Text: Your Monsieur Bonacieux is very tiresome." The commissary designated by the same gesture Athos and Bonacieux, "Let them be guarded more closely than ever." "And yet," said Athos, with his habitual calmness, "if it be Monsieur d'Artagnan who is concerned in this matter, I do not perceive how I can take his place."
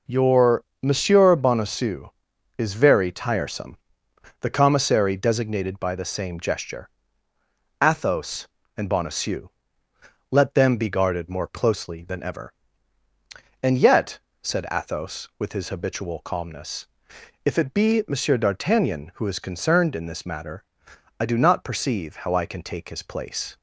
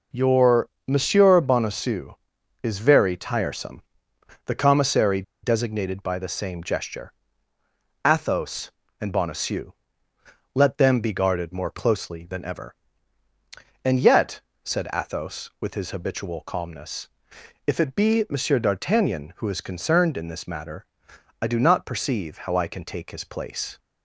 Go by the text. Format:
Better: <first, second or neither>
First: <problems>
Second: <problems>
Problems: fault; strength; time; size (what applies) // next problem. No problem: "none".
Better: first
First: pauses between "Your" and "Monsieur"; slight; at 0.6 s; 0.18 s long // pauses between "gesture" and "Athos"; noticeable; at 6.8 s; 0.92 s long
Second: pauses between "Your" and "Monsieur"; slight; at 0.6 s; 0.18 s long // pauses between "commissary" and "designated"; slight; at 5.2 s; 0.21 s long // pauses between "gesture" and "Athos"; noticeable; at 7.1 s; 0.92 s long